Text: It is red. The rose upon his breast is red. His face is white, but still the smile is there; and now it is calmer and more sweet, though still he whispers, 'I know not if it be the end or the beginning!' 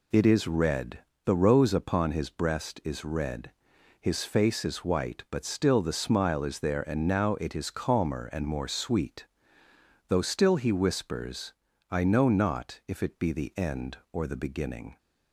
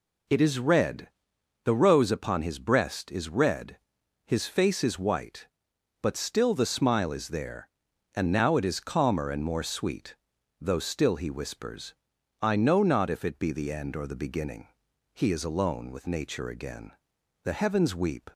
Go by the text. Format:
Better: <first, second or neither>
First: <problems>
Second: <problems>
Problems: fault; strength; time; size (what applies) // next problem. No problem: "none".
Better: first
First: none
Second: goes on to say "He is alone with Nature again The heavens weep"; strong; from 15.1 s on; 3.1 s long